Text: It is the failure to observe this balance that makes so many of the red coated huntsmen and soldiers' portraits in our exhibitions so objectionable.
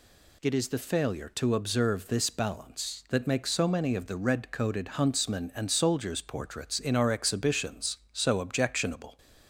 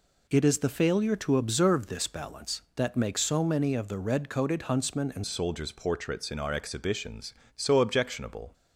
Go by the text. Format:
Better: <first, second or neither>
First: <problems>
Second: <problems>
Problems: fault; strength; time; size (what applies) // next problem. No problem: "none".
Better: first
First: none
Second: changes voice at "soldiers"; from 5.2 s on; 3.3 s long